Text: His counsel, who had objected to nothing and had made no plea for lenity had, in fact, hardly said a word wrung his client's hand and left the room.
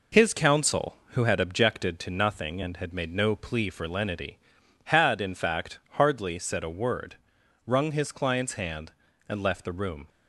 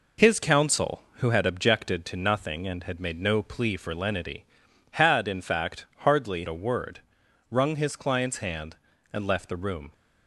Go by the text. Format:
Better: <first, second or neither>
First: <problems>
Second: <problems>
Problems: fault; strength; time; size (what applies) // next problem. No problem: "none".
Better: first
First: pauses between "word" and "wrung"; noticeable; at 7.1 s; 0.48 s long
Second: skips "said"; at 6.4 s // pauses between "word" and "wrung"; noticeable; at 7.0 s; 0.48 s long